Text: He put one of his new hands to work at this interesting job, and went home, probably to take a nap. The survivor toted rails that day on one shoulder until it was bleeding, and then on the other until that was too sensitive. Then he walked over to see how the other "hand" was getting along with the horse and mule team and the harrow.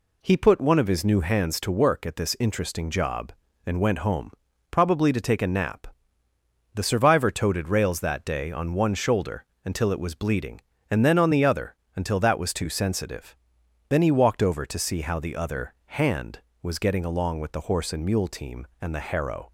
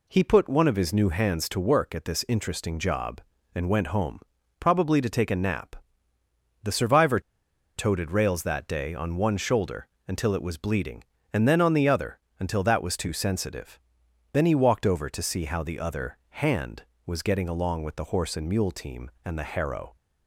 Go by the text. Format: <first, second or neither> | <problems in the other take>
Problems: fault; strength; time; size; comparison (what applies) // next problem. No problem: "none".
first | pauses between "survivor" and "toted"; noticeable; at 7.1 s; 0.57 s long // pauses between "shoulder" and "until"; slight; at 9.8 s; 0.20 s long; slight in the first // pauses between "other" and "until"; slight; at 12.1 s; 0.20 s long; slight in the first